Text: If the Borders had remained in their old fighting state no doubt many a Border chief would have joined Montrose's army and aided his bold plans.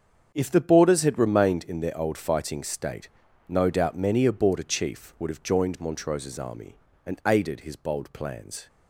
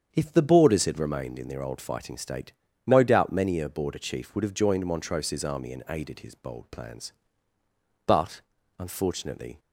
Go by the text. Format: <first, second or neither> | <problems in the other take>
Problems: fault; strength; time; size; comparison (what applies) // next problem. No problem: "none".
first | starts louder than the rest; strong; until 1.1 s; 7.5 dB; strong in the first // pauses between "state" and "no"; slight; at 2.5 s; 0.36 s long; also in the first // goes on to say "But unfortunately"; from 8.0 s on; 1.5 s long